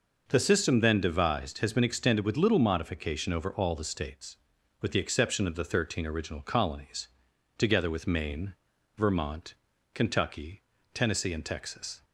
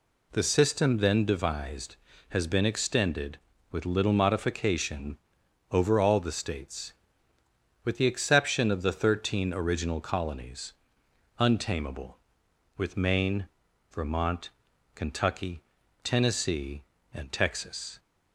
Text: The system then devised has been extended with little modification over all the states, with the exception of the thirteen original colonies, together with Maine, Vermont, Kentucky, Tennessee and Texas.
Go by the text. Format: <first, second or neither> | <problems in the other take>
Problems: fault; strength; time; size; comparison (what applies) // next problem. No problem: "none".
first | pauses between "modification" and "over"; noticeable; at 5.1 s; 0.54 s long // says "untamable" for "together"; at 11.3 s